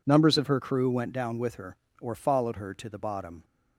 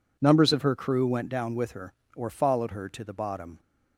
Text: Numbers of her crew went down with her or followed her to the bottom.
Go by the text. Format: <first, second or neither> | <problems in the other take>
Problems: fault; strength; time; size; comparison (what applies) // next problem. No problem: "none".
neither | none